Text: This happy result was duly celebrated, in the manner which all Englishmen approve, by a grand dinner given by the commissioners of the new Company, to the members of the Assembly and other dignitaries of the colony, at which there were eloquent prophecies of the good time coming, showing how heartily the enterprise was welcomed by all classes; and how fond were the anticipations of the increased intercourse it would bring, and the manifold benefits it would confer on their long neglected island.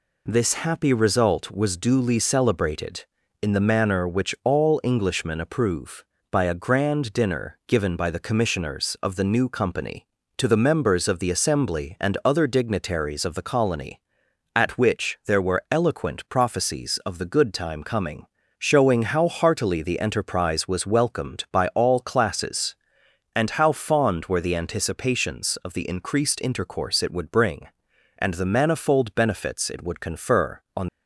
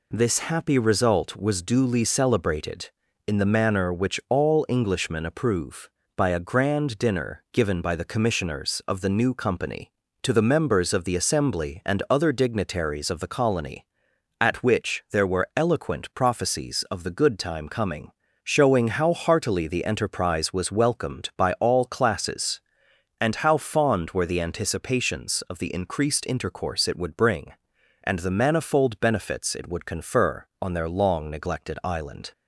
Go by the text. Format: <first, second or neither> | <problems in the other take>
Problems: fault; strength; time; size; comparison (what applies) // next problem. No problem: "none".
second | stops before "their long neglected island"; at 30.8 s